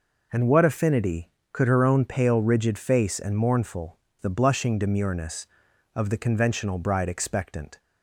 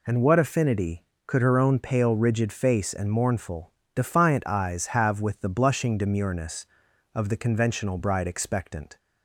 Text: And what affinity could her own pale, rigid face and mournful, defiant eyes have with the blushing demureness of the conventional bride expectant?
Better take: second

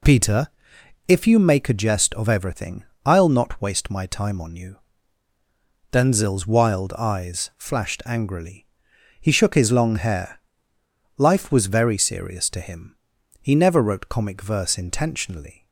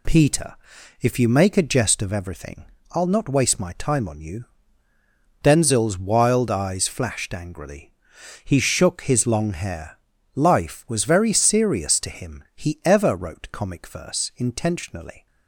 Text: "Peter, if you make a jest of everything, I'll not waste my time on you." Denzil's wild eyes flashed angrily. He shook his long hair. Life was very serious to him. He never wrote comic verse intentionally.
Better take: first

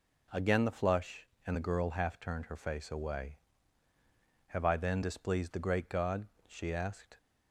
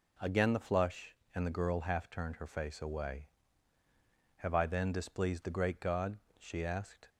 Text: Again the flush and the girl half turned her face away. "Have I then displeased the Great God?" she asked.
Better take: neither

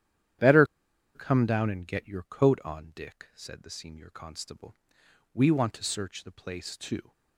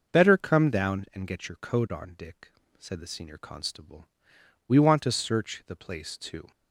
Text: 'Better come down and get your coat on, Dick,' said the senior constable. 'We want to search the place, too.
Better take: second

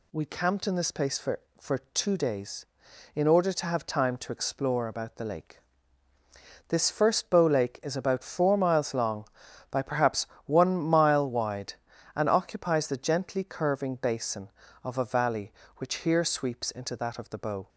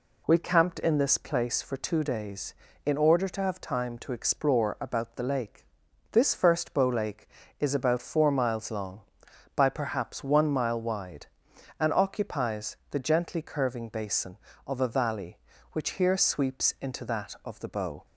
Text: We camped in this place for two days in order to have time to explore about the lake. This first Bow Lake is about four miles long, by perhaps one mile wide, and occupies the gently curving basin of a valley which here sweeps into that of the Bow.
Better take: second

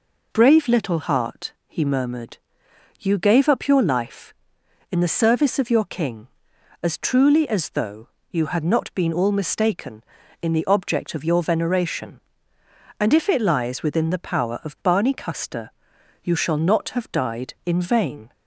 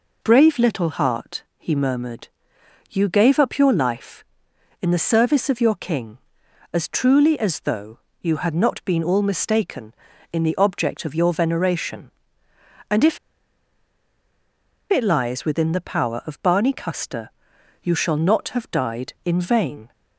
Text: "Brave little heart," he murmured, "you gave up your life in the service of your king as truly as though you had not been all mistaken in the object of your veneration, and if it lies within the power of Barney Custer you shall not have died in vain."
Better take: first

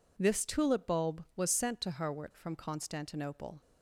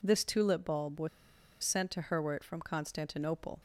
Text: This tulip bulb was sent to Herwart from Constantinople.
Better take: first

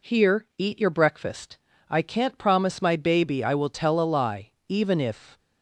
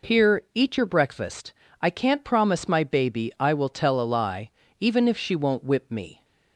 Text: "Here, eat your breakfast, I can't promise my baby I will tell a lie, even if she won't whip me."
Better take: second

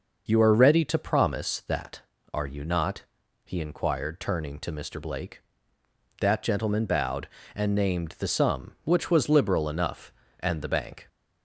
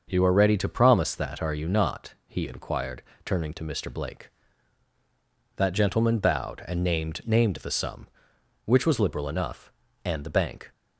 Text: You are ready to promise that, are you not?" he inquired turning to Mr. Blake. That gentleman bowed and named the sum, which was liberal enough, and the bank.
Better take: first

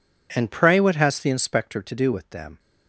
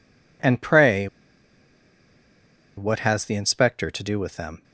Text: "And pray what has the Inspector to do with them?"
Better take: first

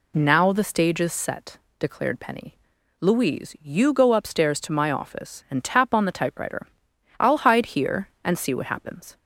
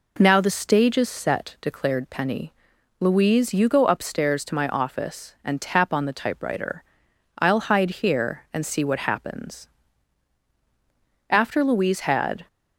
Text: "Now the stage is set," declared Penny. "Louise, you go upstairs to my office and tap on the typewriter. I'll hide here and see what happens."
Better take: first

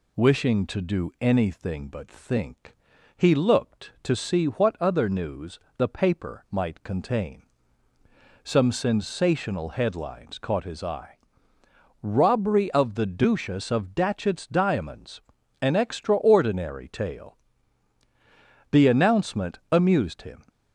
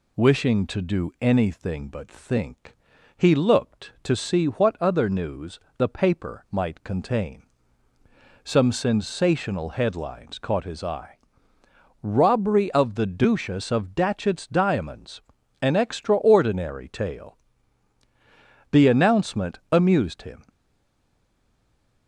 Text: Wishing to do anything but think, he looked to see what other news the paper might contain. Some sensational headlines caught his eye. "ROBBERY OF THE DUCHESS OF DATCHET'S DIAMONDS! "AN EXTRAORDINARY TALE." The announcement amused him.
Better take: first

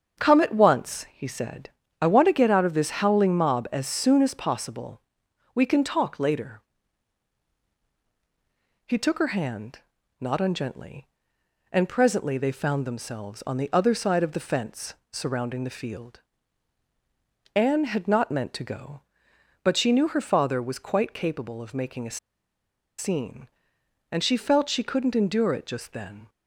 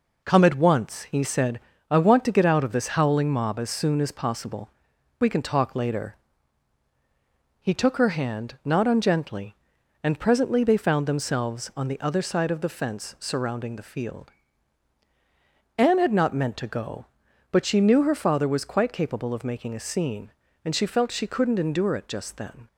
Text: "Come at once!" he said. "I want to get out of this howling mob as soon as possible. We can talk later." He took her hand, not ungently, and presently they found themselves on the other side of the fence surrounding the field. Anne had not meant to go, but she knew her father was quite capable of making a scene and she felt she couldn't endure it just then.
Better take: second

